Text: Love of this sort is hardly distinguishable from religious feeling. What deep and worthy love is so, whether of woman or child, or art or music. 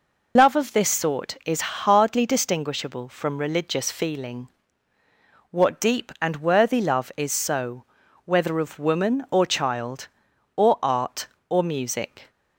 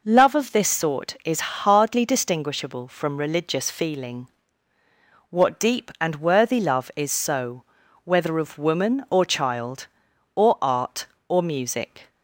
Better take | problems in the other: second | loses the start of "Love"; at 0.3 s; 95 ms

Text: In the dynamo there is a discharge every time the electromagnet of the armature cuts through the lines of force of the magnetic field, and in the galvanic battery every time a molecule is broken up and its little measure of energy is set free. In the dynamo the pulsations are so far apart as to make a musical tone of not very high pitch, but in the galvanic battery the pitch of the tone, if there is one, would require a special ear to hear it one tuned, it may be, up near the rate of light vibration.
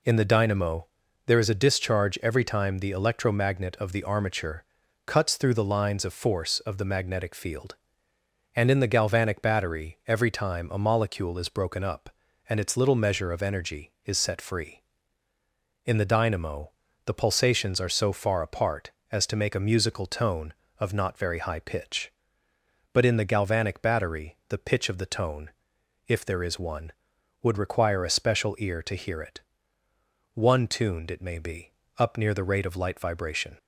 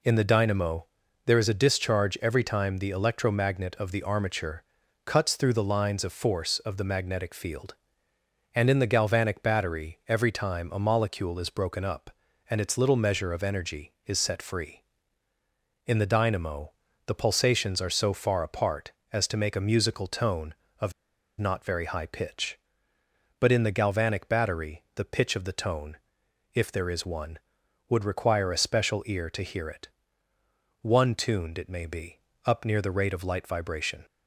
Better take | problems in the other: first | pauses between "dynamo" and "there"; at 0.8 s; 0.40 s long; also in the first // pauses between "armature" and "cuts"; at 4.6 s; 0.42 s long; also in the first // pauses between "dynamo" and "the"; slight; at 16.7 s; 0.34 s long; slight in the first // pauses between "of" and "not"; noticeable; at 20.9 s; 0.48 s long // pauses between "it" and "one"; noticeable; at 29.8 s; 0.94 s long; noticeable in the first

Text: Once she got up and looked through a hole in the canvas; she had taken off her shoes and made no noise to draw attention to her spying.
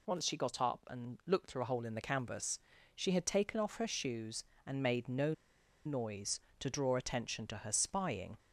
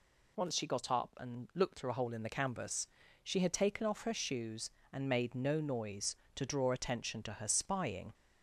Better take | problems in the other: second | pauses between "no" and "noise"; noticeable; at 5.3 s; 0.52 s long

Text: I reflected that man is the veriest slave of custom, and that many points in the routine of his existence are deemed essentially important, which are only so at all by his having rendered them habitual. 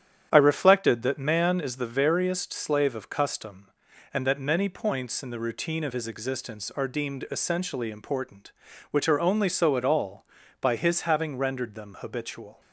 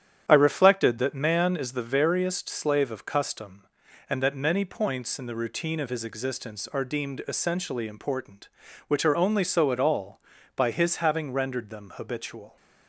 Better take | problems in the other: neither | starts louder than the rest; strong; the same in both

